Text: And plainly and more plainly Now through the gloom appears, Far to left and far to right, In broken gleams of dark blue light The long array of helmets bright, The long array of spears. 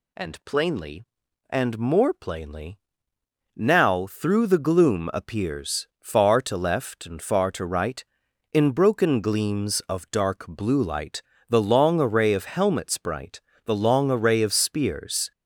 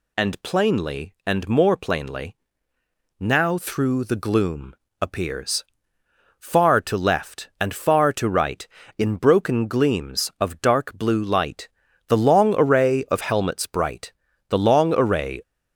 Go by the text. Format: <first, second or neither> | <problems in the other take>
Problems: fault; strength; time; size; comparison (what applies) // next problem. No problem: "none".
first | pauses between "plainly" and "Now"; noticeable; at 2.3 s; 0.82 s long; noticeable in the first // pauses between "gloom" and "appears"; slight; at 4.7 s; 0.26 s long // pauses between "light" and "The"; at 11.6 s; 0.40 s long; slight in the first // stops before "of spears"; at 15.4 s